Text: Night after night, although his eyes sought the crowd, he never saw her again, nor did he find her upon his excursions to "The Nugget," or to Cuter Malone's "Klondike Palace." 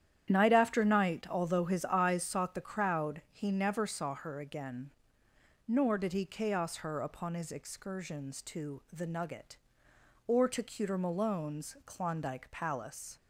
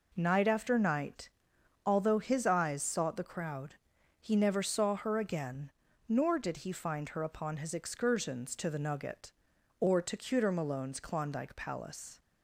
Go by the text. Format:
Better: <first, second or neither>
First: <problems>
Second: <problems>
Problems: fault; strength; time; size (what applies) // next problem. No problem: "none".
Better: second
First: starts louder than the rest; strong; until 1.3 s; 10 dB // says "chaos" for "find"; at 6.2 s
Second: none